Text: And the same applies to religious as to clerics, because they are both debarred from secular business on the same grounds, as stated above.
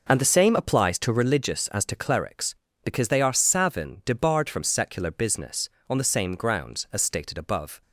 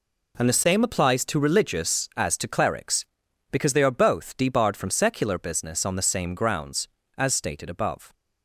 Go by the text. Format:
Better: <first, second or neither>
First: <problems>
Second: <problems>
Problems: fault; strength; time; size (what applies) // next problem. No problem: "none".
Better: second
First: says "savin" for "both"; at 3.3 s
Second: none